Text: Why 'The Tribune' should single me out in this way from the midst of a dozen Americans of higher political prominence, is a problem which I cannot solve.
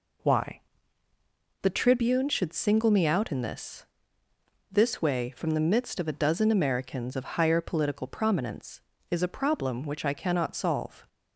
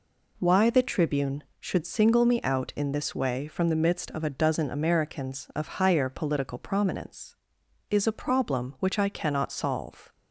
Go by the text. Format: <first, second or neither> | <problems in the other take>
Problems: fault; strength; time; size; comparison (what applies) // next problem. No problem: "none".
second | pauses between "Why" and "The"; at 0.5 s; 1.0 s long // says "this" twice; at 4.7 s